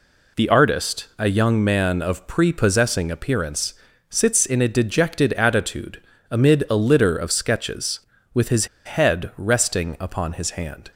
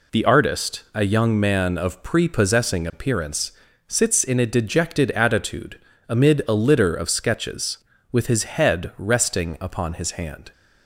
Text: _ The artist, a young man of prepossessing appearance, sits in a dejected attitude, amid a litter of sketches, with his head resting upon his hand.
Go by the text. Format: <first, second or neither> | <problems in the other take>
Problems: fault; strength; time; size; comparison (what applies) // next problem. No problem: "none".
second | pauses between "his" and "head"; slight; at 8.6 s; 0.19 s long